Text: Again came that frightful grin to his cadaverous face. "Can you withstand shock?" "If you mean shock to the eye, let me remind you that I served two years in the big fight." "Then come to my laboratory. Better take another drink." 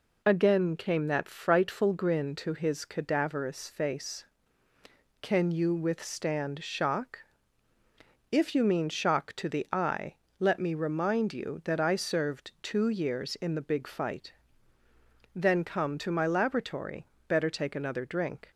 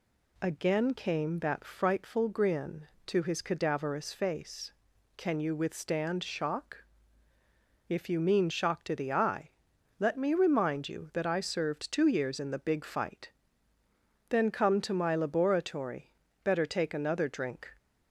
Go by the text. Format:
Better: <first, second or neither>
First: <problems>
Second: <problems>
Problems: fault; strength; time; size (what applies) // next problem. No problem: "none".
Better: neither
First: none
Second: none